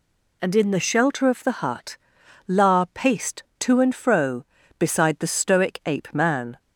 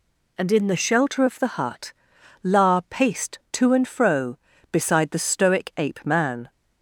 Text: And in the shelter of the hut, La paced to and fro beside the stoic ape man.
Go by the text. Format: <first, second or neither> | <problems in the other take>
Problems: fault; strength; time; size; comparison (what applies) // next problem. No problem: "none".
neither | none